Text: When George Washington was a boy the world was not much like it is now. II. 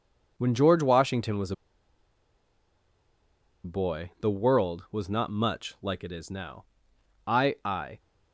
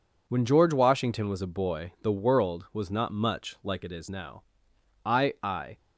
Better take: second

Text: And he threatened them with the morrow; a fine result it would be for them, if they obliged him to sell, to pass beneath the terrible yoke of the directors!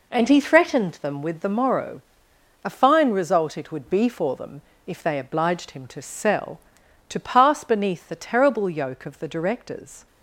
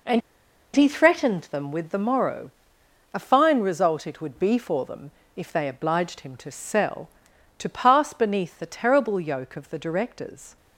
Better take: first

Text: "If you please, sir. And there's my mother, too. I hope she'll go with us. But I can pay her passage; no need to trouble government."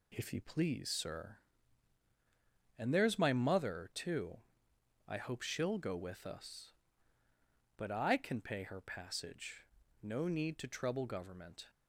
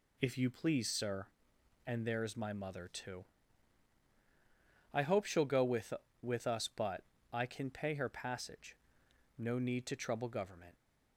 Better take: first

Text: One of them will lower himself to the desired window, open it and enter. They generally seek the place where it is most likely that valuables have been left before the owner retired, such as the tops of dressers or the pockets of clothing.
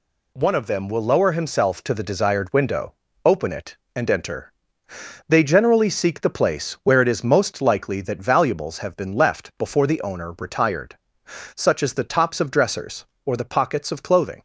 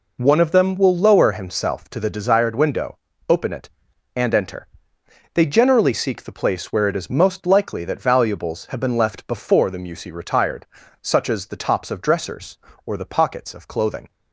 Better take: first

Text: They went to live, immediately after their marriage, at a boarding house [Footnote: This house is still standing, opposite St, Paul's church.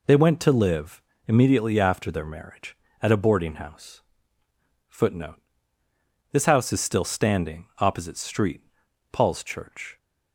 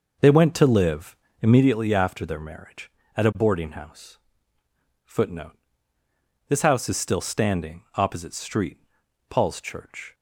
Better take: first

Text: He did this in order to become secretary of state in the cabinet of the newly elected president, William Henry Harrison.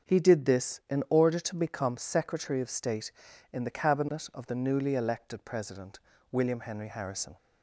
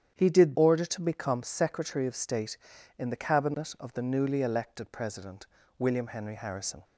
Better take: first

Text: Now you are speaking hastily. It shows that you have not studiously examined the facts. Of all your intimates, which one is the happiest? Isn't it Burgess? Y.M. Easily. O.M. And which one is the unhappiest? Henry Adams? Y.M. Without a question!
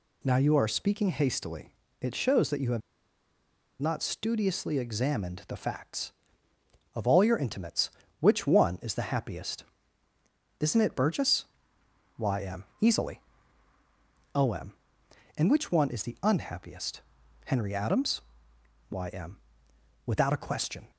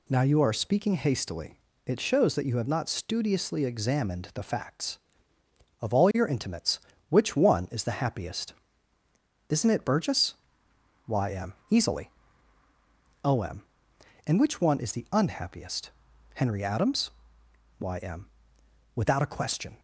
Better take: second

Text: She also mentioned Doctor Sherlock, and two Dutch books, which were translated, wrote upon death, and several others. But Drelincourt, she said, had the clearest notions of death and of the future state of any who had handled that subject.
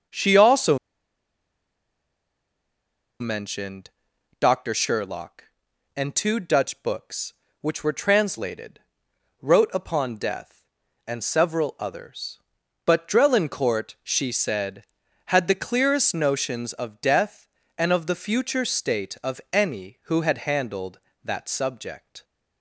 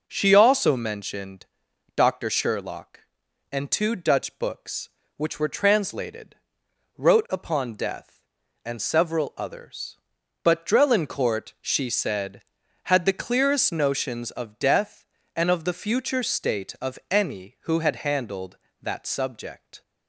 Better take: second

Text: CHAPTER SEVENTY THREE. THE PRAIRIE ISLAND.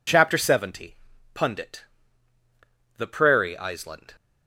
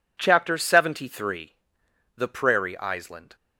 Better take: second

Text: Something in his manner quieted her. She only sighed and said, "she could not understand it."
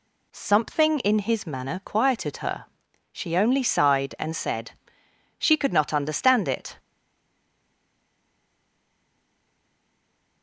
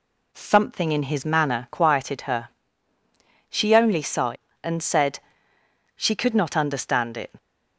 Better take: second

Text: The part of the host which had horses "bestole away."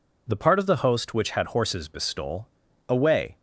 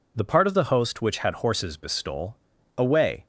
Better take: neither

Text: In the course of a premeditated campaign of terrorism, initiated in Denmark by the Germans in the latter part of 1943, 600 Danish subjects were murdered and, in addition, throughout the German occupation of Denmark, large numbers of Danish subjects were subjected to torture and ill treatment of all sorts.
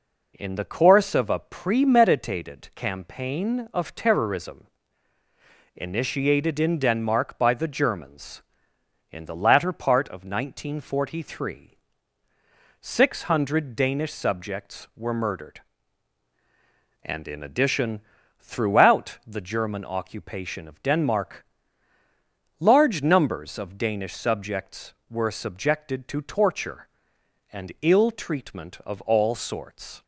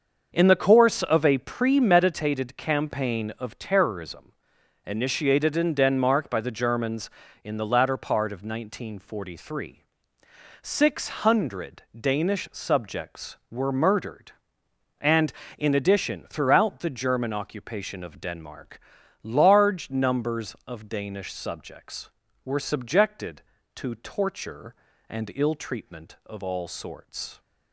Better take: first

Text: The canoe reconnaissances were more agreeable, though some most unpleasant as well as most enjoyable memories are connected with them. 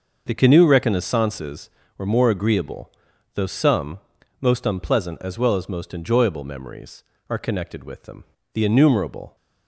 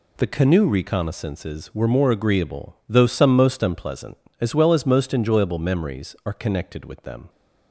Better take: second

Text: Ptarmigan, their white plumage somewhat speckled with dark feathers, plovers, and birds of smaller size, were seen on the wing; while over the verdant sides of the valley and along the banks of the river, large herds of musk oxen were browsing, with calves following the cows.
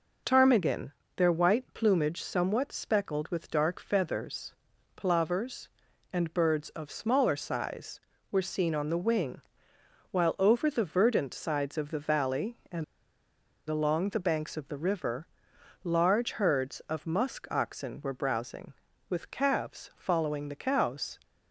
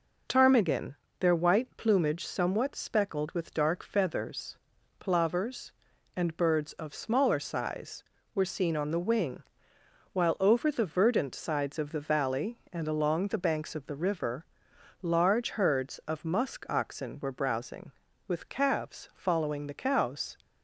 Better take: second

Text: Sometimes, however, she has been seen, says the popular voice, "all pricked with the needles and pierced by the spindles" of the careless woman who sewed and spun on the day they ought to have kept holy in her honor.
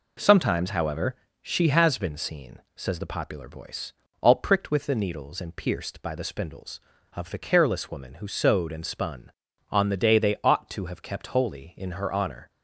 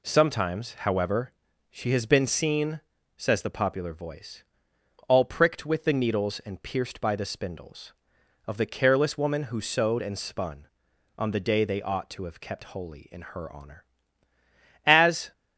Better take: first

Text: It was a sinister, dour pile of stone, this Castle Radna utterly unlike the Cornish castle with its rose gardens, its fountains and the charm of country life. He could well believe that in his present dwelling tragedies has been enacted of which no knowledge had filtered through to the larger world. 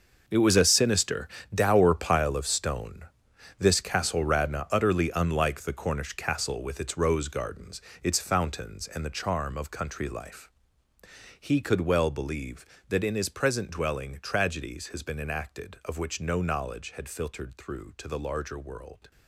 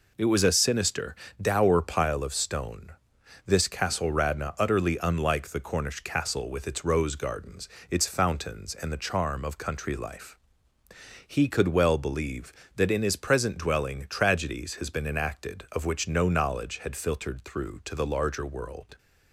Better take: second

